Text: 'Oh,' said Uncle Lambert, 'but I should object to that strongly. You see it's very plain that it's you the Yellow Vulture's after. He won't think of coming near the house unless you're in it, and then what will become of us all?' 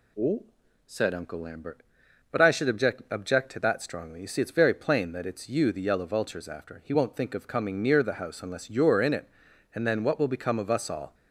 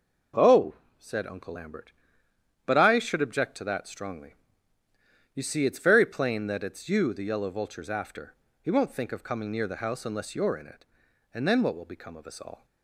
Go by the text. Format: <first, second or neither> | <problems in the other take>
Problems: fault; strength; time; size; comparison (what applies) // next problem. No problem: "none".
second | says "object" twice; at 3.0 s